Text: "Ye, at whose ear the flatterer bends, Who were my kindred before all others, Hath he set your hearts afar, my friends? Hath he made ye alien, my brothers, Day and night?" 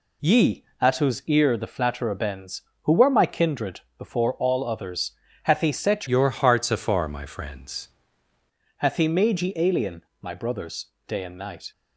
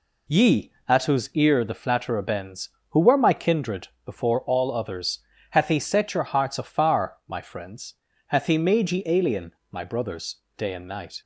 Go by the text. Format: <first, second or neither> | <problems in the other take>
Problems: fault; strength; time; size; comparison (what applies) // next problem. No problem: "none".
second | pauses between "kindred" and "before"; slight; at 3.7 s; 0.18 s long; slight in the second // changes voice from "your" to "friends"; from 6.0 to 7.8 s; 1.8 s long